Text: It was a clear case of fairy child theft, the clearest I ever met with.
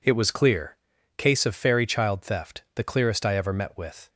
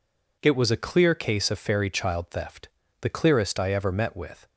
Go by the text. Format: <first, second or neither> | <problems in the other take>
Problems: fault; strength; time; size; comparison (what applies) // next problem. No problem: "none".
second | skips "a"; at 0.3 s // pauses between "clear" and "case"; at 0.7 s; 0.40 s long